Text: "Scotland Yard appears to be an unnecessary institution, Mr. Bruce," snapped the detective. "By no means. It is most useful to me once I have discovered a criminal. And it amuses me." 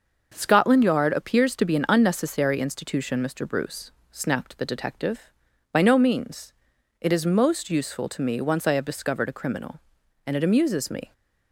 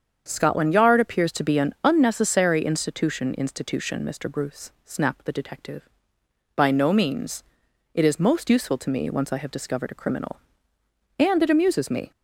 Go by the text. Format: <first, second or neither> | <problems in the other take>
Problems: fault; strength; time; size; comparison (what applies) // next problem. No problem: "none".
first | starts louder than the rest; strong; until 1.2 s; 7.5 dB; noticeable in the first // says "institution" twice; at 3.3 s